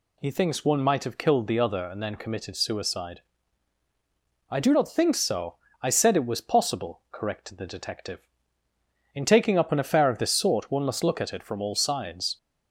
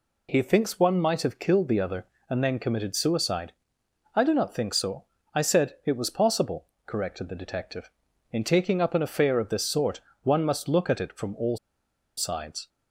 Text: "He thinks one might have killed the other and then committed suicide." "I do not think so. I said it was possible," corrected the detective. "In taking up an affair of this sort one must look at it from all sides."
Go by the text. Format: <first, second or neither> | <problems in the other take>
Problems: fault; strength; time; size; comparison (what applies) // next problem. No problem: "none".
first | pauses between "sort" and "one"; slight; at 10.0 s; 0.20 s long // pauses between "all" and "sides"; noticeable; at 11.5 s; 0.61 s long